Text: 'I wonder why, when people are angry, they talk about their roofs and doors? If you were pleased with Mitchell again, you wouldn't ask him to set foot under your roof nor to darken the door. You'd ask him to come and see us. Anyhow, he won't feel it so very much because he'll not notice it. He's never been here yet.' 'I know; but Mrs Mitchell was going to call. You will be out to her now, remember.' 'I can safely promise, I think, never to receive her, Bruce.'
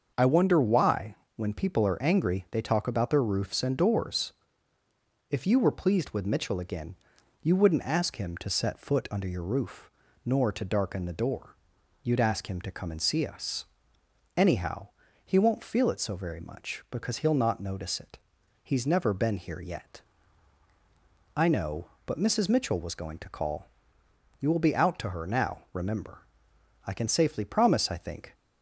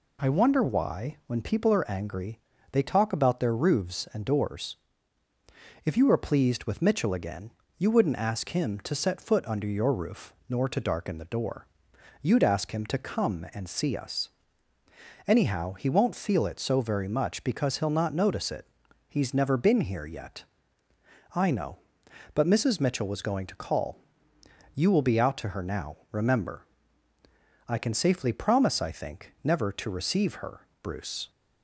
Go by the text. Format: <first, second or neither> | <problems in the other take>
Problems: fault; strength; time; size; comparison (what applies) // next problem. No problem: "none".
second | starts louder than the rest; until 1.1 s; 6.5 dB // pauses between "roof" and "nor"; slight; at 9.8 s; 0.34 s long; slight in the second // stops before "never to receive her Bruce"; at 28.3 s